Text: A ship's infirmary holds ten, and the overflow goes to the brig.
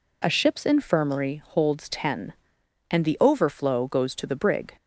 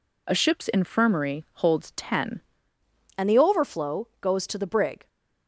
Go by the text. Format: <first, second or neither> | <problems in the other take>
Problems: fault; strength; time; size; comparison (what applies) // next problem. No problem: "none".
first | changes voice at "and"; from 3.1 s on; 1.9 s long